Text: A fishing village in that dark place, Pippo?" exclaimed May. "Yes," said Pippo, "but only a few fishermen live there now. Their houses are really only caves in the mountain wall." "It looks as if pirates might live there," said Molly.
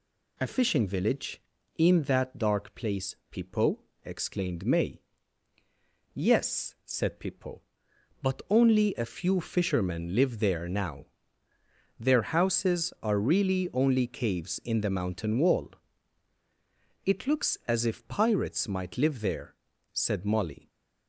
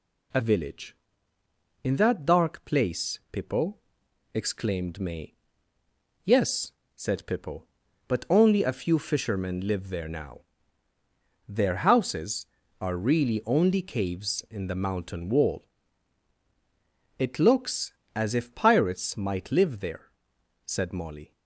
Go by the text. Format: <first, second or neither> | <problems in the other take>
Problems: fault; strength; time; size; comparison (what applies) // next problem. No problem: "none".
first | skips "fishing"; at 0.4 s